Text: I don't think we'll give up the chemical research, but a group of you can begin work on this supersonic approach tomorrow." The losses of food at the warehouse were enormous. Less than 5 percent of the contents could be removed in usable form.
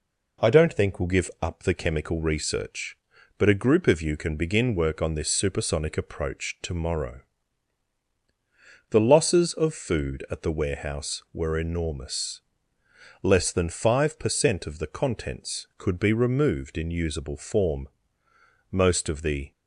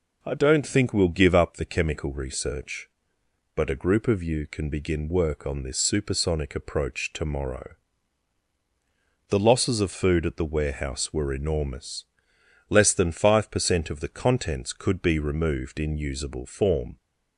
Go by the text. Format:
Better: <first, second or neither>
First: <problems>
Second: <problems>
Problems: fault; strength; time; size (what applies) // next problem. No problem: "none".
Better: second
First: goes on to say "Most of the"; noticeable; from 18.7 s on; 0.80 s long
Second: none